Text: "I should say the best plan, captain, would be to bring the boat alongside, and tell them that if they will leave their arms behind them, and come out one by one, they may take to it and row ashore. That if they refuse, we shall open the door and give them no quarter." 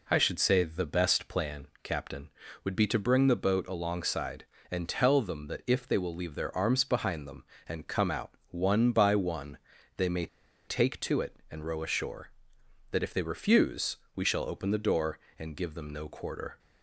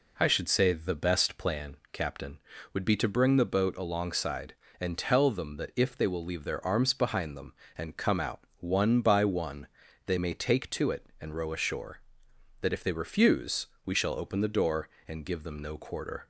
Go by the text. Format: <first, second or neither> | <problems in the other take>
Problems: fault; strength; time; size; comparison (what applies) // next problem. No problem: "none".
second | pauses between "may" and "take"; at 10.2 s; 0.40 s long